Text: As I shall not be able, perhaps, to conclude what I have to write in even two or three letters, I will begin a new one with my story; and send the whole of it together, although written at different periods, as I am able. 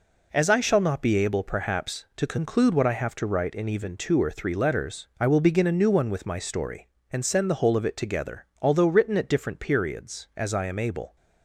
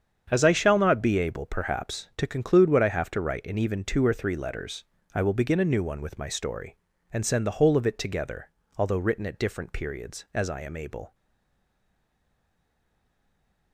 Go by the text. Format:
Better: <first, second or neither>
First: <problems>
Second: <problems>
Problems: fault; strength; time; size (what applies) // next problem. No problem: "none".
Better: first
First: none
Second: starts louder than the rest; strong; until 1.3 s; 7.5 dB // stays silent after the last word; strong; from 11.1 s on; 2.6 s long